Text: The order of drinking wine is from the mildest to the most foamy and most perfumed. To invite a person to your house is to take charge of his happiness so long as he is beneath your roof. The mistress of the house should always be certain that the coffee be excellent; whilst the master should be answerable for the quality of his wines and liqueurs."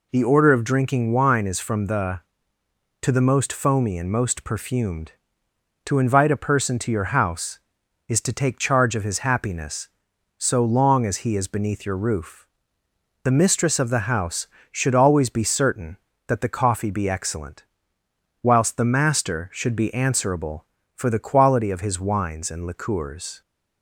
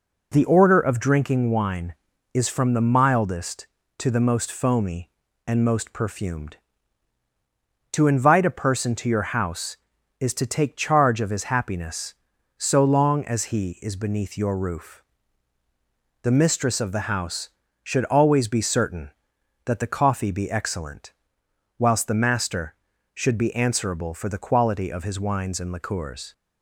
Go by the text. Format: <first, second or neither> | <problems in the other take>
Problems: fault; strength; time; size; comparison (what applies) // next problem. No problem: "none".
second | skips "mildest"; at 2.6 s